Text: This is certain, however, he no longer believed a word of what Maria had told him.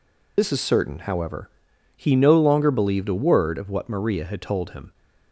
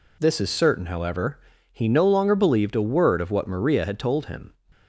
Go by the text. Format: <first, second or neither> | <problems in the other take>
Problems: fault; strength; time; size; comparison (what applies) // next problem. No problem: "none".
second | loses the start of "This"; at 0.3 s; 45 ms